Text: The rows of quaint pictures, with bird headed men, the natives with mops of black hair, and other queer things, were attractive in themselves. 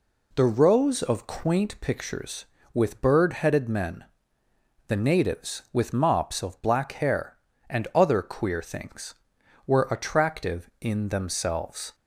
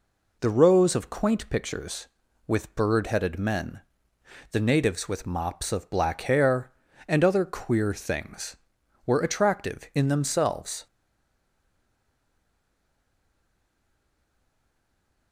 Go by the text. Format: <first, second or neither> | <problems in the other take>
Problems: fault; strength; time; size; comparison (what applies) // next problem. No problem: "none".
first | stays silent after the last word; strong; from 10.8 s on; 4.5 s long